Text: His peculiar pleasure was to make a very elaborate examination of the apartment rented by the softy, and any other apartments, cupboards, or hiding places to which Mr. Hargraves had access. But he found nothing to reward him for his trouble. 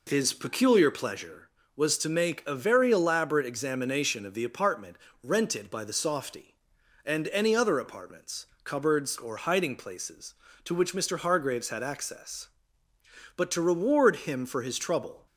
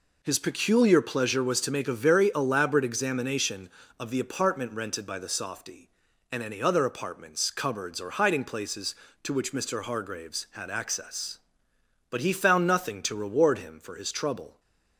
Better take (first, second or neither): second